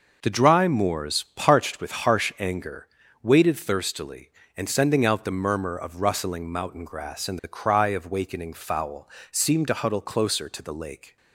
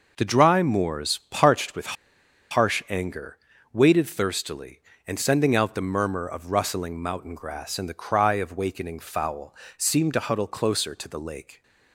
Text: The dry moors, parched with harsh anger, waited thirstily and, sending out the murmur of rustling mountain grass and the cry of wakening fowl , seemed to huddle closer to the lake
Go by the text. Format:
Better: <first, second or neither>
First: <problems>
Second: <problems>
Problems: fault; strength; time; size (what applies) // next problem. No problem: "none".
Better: first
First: none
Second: pauses between "with" and "harsh"; noticeable; at 1.9 s; 0.57 s long